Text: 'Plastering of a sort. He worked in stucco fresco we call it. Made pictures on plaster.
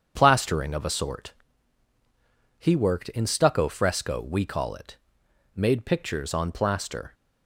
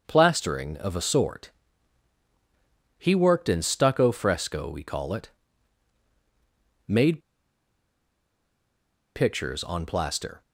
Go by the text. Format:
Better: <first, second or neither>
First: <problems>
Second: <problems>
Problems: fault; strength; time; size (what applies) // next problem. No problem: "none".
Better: first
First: starts louder than the rest; strong; until 1.1 s; 7.5 dB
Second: starts louder than the rest; until 1.0 s; 6.5 dB // pauses between "Made" and "pictures"; strong; at 7.1 s; 1.9 s long